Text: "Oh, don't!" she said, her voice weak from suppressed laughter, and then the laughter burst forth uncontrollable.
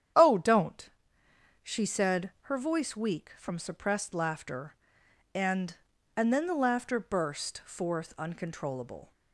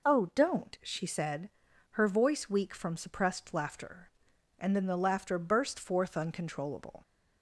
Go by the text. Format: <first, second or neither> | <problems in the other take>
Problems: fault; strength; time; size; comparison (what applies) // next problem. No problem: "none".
second | starts louder than the rest; strong; until 1.8 s; 9 dB // says "and" twice; at 6.1 s